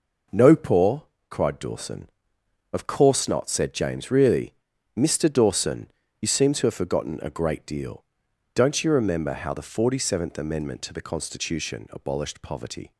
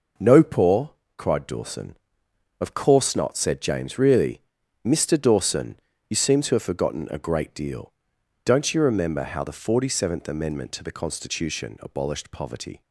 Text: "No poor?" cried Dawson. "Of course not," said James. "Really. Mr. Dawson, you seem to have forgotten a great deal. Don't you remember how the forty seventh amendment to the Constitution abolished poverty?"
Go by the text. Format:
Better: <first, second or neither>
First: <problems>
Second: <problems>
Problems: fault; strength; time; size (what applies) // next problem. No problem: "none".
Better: neither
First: none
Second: none